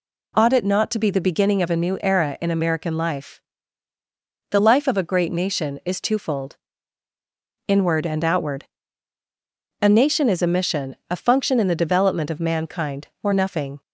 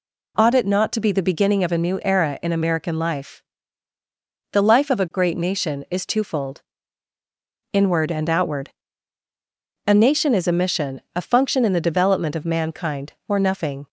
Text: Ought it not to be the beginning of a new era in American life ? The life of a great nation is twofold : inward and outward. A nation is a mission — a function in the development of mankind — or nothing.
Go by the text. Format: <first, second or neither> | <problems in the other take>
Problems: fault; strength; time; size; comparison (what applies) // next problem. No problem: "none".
neither | none